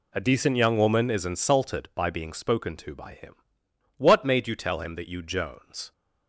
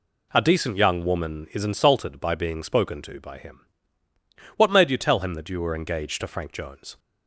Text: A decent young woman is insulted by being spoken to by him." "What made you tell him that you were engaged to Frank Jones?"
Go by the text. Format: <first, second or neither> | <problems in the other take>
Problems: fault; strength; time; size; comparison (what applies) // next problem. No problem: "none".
second | skips "were engaged to Frank"; at 5.2 s